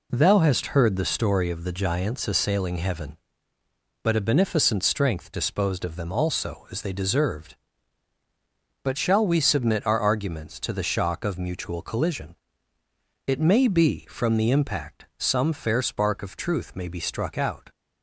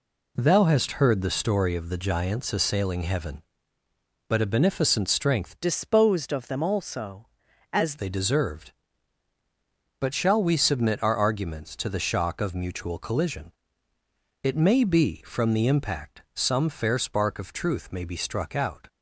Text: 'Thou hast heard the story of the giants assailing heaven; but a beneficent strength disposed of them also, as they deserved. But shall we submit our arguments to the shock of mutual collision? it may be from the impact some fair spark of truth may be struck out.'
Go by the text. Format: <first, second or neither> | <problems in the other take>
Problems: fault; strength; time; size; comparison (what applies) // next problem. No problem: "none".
first | changes voice from "disposed" to "as"; from 5.5 to 7.9 s; 2.4 s long